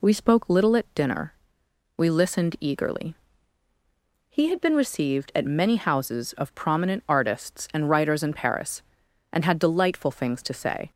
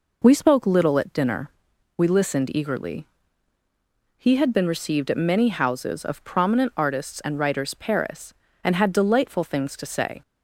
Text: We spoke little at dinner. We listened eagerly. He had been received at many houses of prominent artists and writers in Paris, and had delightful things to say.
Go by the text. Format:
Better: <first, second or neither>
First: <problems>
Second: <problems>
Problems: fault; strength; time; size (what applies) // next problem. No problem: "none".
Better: first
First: none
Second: skips "in"; at 7.7 s